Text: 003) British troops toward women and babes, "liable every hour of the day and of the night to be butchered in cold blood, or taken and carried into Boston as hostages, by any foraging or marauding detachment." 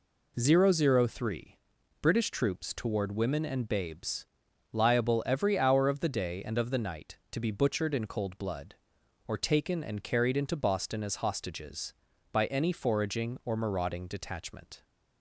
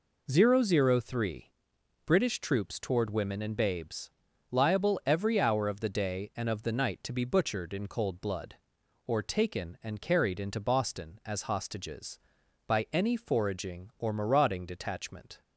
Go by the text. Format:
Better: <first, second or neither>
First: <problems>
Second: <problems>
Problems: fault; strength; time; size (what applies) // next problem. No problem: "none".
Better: neither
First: none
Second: none